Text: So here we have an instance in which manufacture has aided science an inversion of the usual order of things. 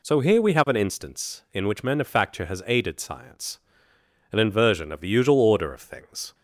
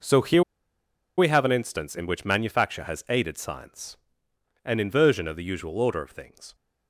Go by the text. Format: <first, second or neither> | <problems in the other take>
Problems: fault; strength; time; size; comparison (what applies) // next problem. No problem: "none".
first | pauses between "here" and "we"; noticeable; at 0.4 s; 0.75 s long // pauses between "science" and "an"; noticeable; at 3.9 s; 0.72 s long; noticeable in the first